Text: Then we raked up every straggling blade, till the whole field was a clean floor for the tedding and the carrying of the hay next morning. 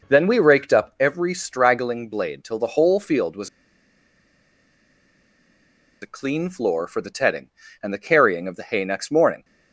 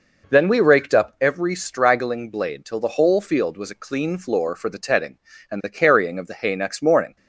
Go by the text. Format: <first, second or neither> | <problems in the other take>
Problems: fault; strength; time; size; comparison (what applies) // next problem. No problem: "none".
second | pauses between "was" and "a"; strong; at 3.4 s; 2.5 s long